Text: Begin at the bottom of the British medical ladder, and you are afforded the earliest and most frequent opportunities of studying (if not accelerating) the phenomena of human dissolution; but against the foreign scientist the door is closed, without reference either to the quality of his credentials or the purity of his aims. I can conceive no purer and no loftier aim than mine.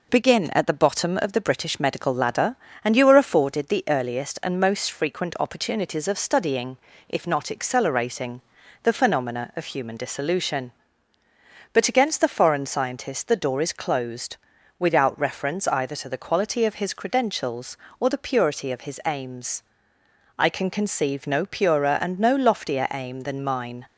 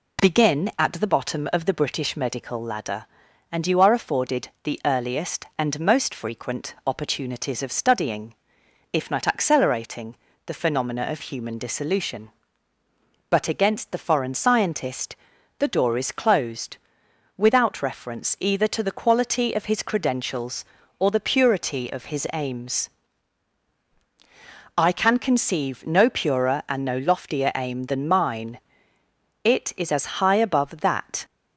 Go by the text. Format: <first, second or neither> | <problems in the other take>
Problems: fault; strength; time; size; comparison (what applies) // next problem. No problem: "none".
first | pauses between "scientist" and "the"; at 15.1 s; 0.42 s long // goes on to say "It is as high above that"; strong; from 29.4 s on; 1.8 s long